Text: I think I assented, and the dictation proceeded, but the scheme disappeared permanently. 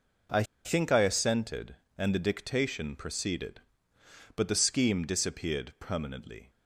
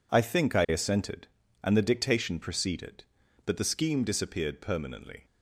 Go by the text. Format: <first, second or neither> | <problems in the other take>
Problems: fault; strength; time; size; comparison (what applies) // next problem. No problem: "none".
second | pauses between "I" and "think"; slight; at 0.4 s; 0.20 s long